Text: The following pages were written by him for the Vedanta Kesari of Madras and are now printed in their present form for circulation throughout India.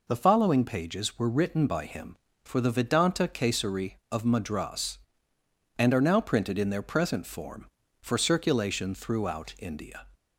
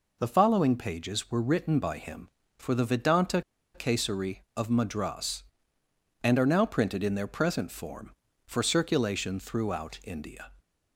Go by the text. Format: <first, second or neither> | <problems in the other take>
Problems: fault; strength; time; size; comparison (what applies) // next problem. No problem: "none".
first | pauses between "Vedanta" and "Kesari"; slight; at 3.4 s; 0.34 s long